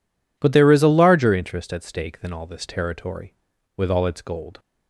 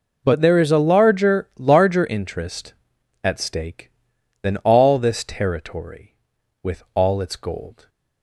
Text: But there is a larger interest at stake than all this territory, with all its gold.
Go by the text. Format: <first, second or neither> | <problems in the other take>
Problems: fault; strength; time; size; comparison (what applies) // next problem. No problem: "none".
first | says "larger" twice; at 1.5 s